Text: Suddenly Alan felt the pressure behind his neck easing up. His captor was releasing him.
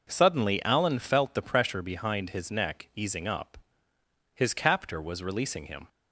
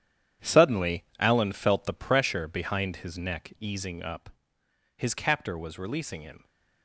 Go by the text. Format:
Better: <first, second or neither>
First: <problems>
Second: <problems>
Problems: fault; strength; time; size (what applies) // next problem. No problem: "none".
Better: first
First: none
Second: gets quieter; strong; throughout; 11.5 dB // pauses between "Suddenly" and "Alan"; slight; at 1.0 s; 0.16 s long